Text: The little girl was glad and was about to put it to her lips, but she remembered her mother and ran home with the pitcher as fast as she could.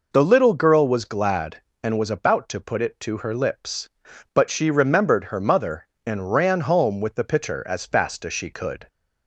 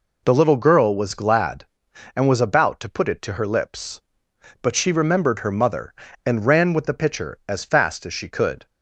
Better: first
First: none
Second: skips "home"; at 6.7 s

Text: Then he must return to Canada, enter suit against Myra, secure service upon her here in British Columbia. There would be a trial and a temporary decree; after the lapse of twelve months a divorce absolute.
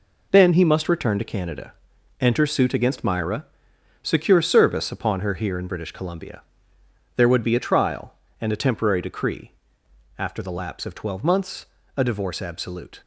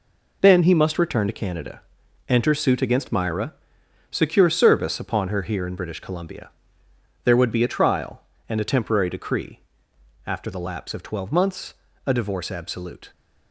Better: neither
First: pauses between "months" and "a"; slight; at 11.6 s; 0.30 s long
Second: pauses between "months" and "a"; slight; at 11.7 s; 0.32 s long

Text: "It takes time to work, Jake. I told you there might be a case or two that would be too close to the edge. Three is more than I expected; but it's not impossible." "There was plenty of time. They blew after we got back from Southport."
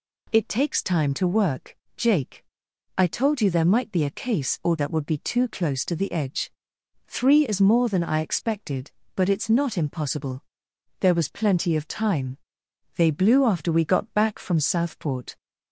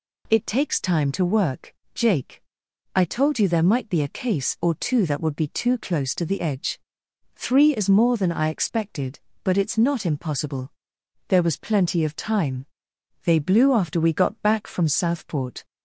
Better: second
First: skips "two"; at 4.7 s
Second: none

